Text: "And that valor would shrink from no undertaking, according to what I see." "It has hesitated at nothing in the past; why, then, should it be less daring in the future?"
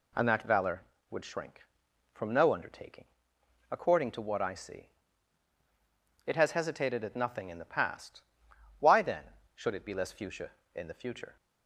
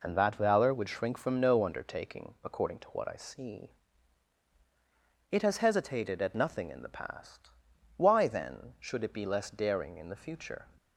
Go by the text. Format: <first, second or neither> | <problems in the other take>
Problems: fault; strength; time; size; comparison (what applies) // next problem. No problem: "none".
second | says "fuchsia" for "daring"; at 10.1 s